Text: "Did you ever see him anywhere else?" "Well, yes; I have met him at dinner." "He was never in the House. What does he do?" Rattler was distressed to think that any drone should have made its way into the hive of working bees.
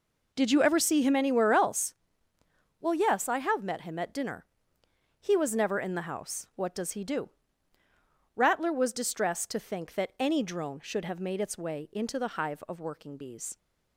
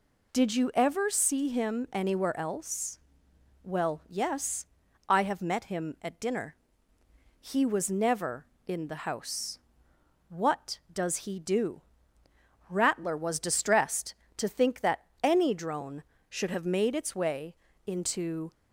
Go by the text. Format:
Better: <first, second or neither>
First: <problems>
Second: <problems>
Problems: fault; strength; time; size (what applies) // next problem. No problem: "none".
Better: first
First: none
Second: pauses between "that" and "any"; slight; at 15.0 s; 0.16 s long // pauses between "way" and "into"; slight; at 17.5 s; 0.30 s long // stops before "the hive of working bees"; at 18.5 s